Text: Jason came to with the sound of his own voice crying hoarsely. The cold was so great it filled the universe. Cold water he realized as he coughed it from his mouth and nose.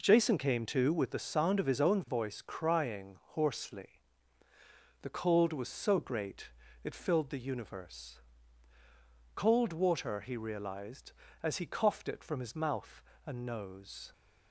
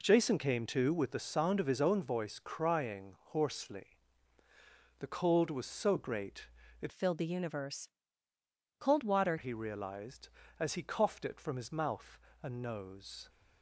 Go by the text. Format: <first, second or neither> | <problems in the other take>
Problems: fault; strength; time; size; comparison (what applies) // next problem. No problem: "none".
first | pauses between "great" and "it"; slight; at 6.4 s; 0.34 s long; slight in the first // changes voice from "filled" to "water"; from 6.9 to 9.3 s; 2.4 s long